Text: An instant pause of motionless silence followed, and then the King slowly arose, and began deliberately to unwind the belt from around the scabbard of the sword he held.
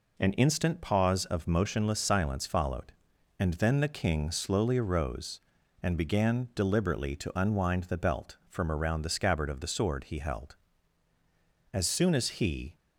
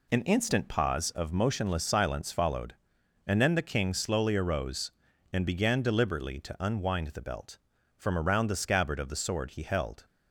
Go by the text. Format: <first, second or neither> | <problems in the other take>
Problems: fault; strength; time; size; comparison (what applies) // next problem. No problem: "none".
second | goes on to say "As soon as he"; noticeable; from 11.7 s on; 1.0 s long